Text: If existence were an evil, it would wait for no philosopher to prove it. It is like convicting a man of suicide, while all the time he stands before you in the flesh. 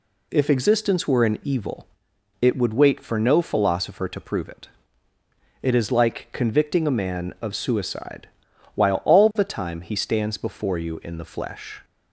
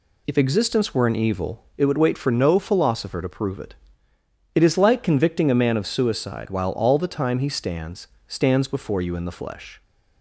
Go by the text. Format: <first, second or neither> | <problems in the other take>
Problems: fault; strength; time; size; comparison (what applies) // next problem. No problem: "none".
first | says "stands" twice; at 8.2 s